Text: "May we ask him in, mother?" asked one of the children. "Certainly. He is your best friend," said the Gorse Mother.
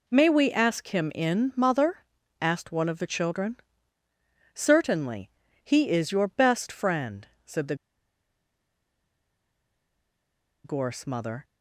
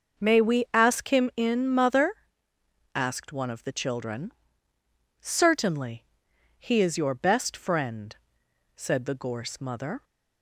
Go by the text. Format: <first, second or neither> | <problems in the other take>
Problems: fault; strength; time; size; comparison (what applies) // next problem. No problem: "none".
second | pauses between "the" and "Gorse"; strong; at 7.7 s; 2.8 s long